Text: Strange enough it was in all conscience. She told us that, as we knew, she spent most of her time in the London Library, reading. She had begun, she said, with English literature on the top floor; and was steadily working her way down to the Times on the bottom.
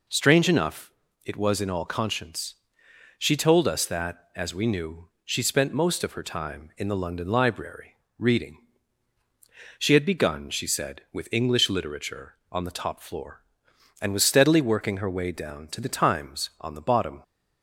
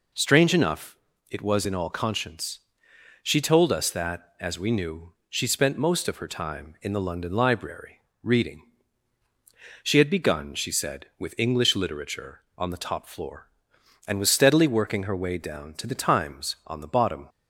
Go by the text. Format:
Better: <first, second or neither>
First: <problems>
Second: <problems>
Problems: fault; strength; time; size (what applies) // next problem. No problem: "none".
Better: neither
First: pauses between "enough" and "it"; slight; at 0.9 s; 0.34 s long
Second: pauses between "enough" and "it"; slight; at 0.9 s; 0.34 s long